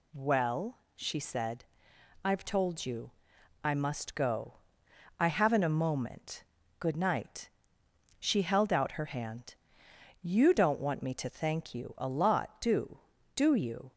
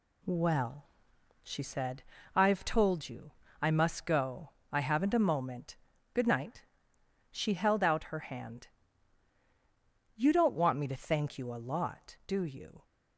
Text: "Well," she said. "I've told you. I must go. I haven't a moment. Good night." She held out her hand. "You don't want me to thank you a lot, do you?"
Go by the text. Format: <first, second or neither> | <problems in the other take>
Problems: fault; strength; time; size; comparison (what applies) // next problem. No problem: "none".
second | says "do" twice; at 13.3 s